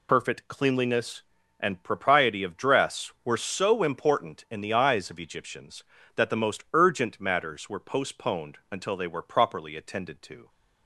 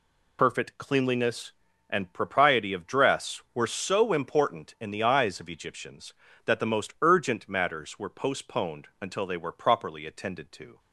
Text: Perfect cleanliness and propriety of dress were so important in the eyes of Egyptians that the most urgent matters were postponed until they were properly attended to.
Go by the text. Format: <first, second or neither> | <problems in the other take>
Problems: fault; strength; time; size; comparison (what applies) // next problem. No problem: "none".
neither | none